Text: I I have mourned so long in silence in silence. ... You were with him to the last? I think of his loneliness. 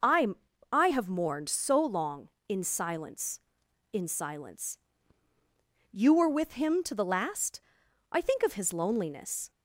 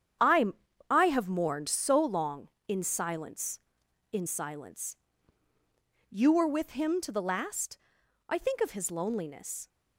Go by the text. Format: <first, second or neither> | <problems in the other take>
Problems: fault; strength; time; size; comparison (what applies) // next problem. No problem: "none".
first | gets quieter; strong; throughout; 9 dB // pauses between "I" and "I"; at 0.4 s; 0.44 s long; also in the first